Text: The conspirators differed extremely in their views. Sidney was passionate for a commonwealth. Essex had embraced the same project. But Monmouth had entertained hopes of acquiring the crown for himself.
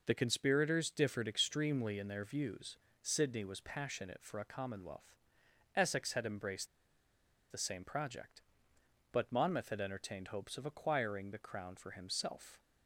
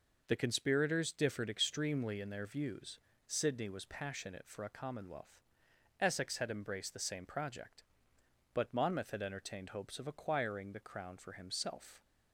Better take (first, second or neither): second